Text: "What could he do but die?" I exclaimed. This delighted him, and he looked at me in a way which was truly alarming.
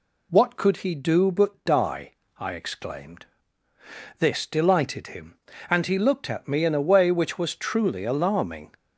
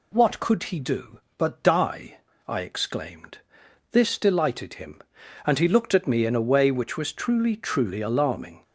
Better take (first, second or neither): first